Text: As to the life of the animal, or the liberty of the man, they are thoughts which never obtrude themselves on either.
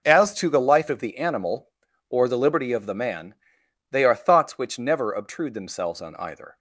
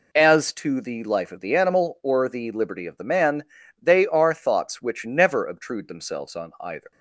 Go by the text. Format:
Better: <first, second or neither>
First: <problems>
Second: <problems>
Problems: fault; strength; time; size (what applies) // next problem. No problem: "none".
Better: neither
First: none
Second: none